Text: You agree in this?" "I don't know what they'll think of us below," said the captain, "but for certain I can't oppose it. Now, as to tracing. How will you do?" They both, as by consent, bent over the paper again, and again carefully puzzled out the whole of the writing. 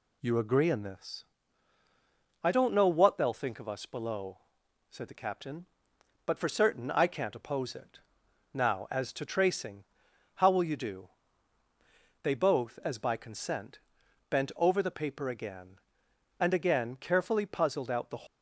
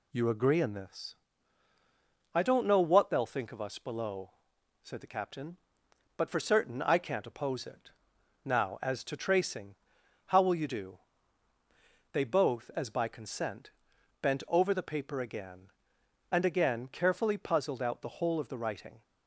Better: second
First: stops before "whole of the writing"; at 18.2 s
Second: none

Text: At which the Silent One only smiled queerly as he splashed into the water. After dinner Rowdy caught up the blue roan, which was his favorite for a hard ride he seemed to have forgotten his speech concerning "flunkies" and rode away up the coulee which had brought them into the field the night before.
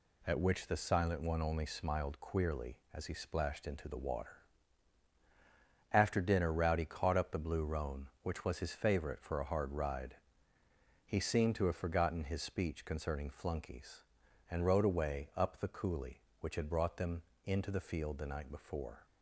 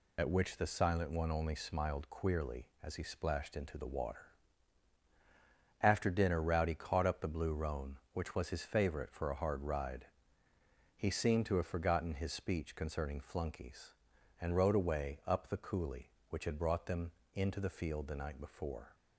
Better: first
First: pauses between "ride" and "he"; noticeable; at 10.1 s; 0.88 s long // pauses between "them" and "into"; slight; at 17.2 s; 0.22 s long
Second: loses the start of "At"; at 0.1 s; 70 ms // pauses between "ride" and "he"; noticeable; at 10.0 s; 0.88 s long // pauses between "them" and "into"; slight; at 17.1 s; 0.22 s long

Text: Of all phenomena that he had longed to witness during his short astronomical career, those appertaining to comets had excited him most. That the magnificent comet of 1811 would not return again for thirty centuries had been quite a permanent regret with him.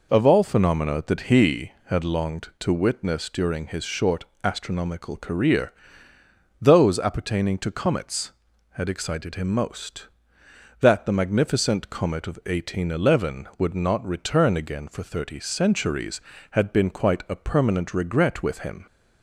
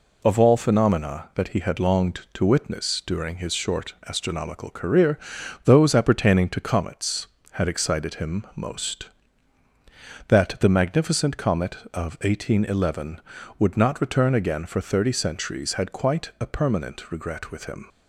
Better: first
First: pauses between "short" and "astronomical"; slight; at 4.2 s; 0.18 s long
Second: pauses between "short" and "astronomical"; slight; at 3.9 s; 0.16 s long // skips "been"; at 15.9 s

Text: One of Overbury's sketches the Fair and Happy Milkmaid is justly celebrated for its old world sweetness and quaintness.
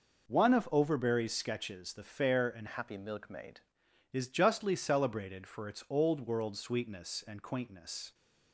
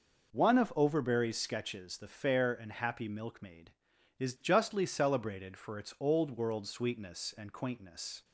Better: second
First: changes voice from "Happy" to "Milkmaid"; from 2.6 to 3.6 s; 1.0 s long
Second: none

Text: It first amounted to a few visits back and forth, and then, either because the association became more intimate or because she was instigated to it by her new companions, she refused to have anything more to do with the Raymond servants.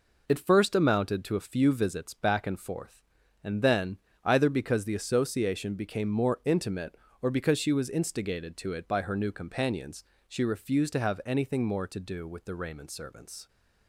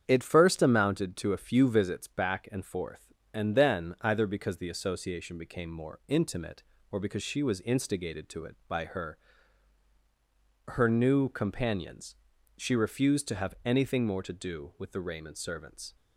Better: first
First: none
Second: starts louder than the rest; strong; until 1.0 s; 8 dB // says "her" twice; at 10.6 s

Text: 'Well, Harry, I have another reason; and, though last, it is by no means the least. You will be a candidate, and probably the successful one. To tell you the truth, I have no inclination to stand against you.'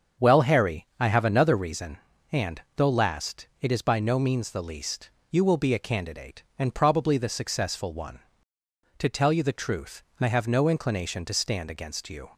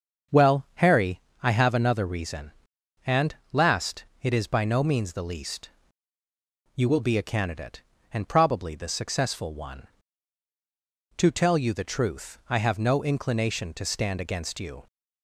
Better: first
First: starts louder than the rest; until 1.3 s; 7 dB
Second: starts louder than the rest; until 1.6 s; 6.5 dB // skips "though"; at 3.4 s

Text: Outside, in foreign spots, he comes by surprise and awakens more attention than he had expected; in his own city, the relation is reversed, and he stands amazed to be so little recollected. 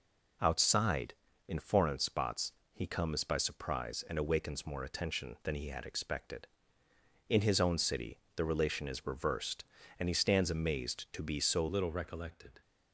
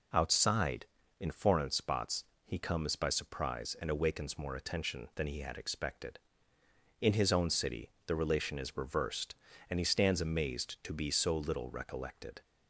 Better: second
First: changes voice at "little"; from 11.6 s on; 1.0 s long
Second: none

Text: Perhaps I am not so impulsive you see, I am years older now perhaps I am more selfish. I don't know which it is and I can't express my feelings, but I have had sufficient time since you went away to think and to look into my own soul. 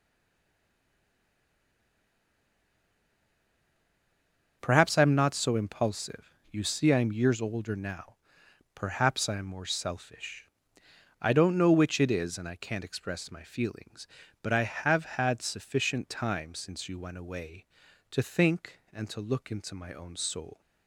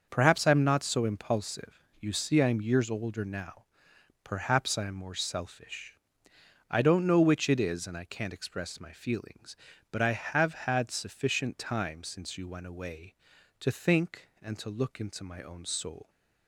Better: second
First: stays silent before the first word; strong; until 4.5 s; 4.5 s long // starts louder than the rest; until 5.6 s; 6.5 dB // pauses between "impulsive" and "you"; slight; at 6.3 s; 0.18 s long // pauses between "now" and "perhaps"; noticeable; at 8.1 s; 0.58 s long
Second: starts louder than the rest; until 1.0 s; 6.5 dB // pauses between "impulsive" and "you"; slight; at 1.8 s; 0.18 s long // pauses between "now" and "perhaps"; noticeable; at 3.6 s; 0.58 s long

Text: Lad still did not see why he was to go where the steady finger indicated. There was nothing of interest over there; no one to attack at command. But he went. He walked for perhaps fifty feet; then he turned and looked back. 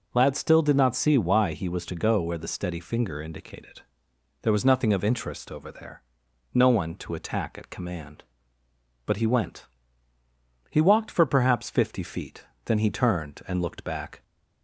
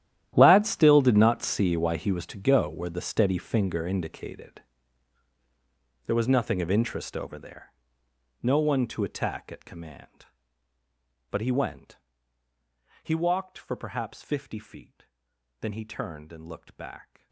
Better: first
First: none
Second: gets quieter; strong; throughout; 19 dB

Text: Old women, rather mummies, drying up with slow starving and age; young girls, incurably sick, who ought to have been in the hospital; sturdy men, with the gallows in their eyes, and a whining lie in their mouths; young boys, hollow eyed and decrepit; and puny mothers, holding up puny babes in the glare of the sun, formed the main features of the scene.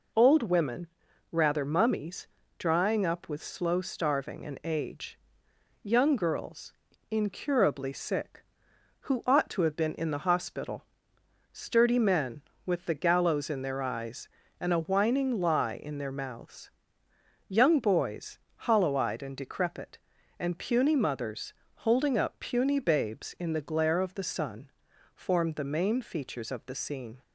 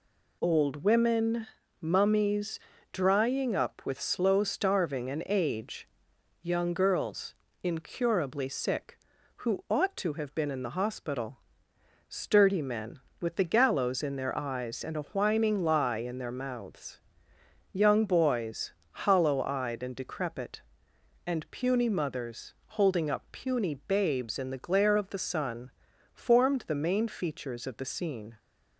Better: first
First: none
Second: skips "rather"; at 1.6 s

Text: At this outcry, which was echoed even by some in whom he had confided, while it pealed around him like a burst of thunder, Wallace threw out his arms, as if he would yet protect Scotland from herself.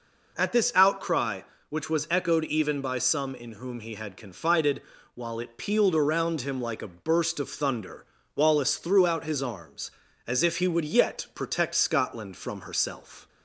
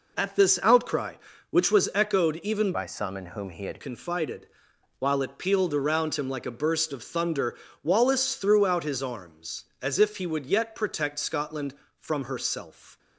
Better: first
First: none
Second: changes voice from "by" to "had"; from 2.7 to 3.8 s; 1.1 s long

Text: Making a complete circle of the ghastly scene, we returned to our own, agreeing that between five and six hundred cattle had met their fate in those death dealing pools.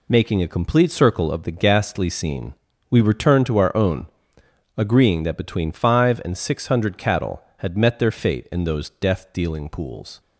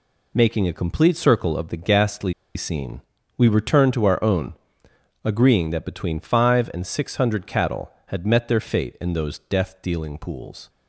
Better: first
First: none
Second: pauses between "ghastly" and "scene"; slight; at 2.3 s; 0.22 s long

